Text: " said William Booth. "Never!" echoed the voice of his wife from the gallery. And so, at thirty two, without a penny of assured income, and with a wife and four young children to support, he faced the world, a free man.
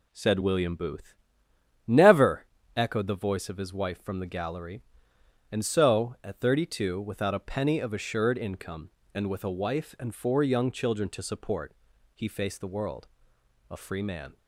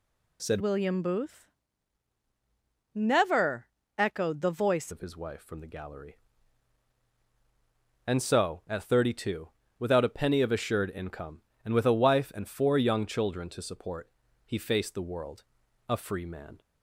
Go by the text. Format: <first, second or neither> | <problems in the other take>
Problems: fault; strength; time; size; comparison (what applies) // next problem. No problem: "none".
first | changes voice from "William" to "voice"; from 0.6 to 4.9 s; 4.3 s long